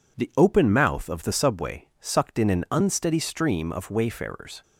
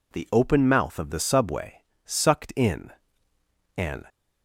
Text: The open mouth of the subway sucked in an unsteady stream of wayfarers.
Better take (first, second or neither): first